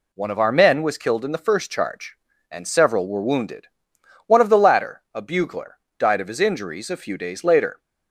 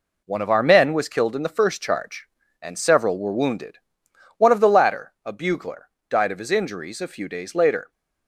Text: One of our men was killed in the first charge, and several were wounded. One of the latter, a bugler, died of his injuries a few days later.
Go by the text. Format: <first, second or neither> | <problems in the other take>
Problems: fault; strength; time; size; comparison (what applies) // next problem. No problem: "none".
first | gets quieter; throughout; 6.5 dB